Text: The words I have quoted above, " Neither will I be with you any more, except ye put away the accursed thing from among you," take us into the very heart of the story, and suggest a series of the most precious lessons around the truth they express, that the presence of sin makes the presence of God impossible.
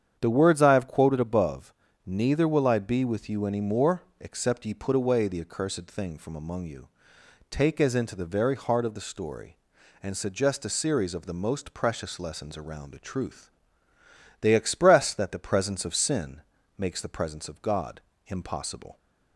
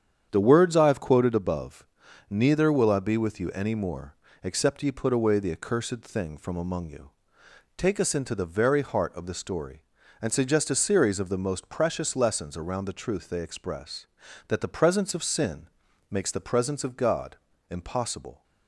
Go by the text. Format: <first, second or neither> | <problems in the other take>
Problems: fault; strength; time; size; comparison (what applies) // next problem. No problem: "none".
second | starts louder than the rest; strong; until 1.2 s; 8.5 dB; strong in the second // says "as" for "us"; at 7.7 s // pauses between "truth" and "they"; noticeable; at 13.5 s; 0.88 s long // pauses between "sin" and "makes"; at 16.4 s; 0.38 s long; also in the second // pauses between "God" and "impossible"; slight; at 17.9 s; 0.26 s long; slight in the second